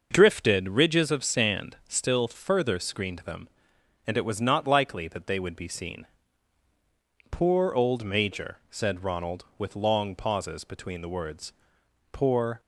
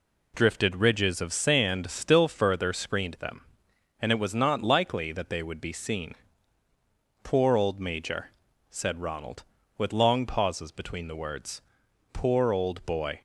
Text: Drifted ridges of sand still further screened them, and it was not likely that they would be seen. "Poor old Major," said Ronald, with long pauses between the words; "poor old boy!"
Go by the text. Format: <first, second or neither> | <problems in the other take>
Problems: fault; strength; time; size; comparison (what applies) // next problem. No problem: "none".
second | starts louder than the rest; noticeable; until 1.1 s; 6 dB // stops before "old boy"; at 12.5 s